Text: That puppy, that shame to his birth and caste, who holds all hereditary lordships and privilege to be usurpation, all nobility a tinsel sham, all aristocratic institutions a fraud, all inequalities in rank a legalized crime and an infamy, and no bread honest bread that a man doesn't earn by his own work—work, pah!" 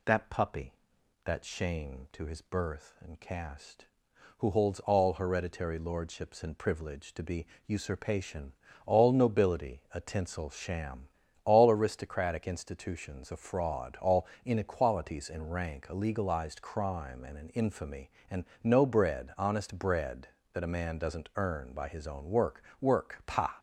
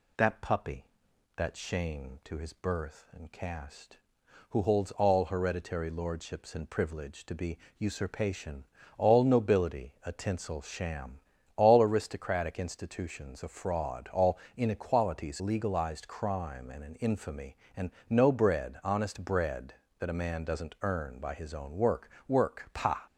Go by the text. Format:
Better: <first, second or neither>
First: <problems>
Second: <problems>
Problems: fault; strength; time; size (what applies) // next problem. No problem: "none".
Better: first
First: pauses between "be" and "usurpation"; slight; at 7.4 s; 0.20 s long // pauses between "all" and "inequalities"; slight; at 14.2 s; 0.20 s long // pauses between "and" and "no"; slight; at 18.4 s; 0.18 s long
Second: pauses between "be" and "usurpation"; slight; at 7.5 s; 0.20 s long // pauses between "all" and "inequalities"; slight; at 14.3 s; 0.20 s long // skips "in rank a"; at 15.3 s // pauses between "and" and "no"; slight; at 17.9 s; 0.18 s long